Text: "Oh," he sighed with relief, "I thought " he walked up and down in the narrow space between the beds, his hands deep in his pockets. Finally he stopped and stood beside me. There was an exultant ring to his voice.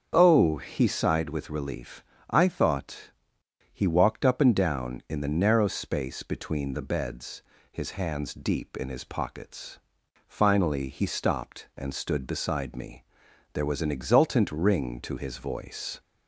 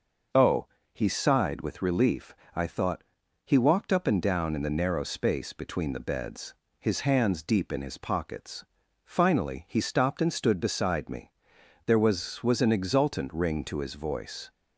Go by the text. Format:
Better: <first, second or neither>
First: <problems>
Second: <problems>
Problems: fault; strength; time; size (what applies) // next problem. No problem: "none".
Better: first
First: starts louder than the rest; until 1.1 s; 6.5 dB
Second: starts louder than the rest; noticeable; until 1.6 s; 6 dB // says "was" twice; at 12.4 s